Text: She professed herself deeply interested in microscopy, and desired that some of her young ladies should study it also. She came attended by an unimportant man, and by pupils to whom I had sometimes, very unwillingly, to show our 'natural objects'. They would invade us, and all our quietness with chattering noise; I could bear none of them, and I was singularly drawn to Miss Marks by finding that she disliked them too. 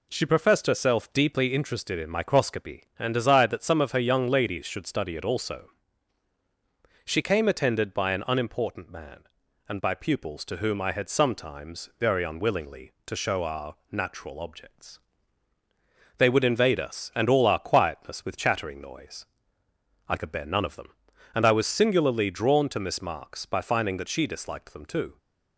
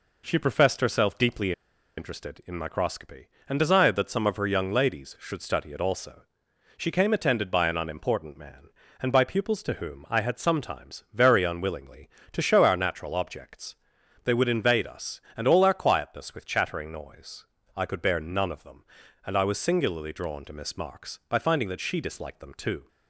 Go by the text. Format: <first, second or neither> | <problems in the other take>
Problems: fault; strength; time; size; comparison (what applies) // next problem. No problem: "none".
first | pauses between "deeply" and "interested"; at 1.5 s; 0.45 s long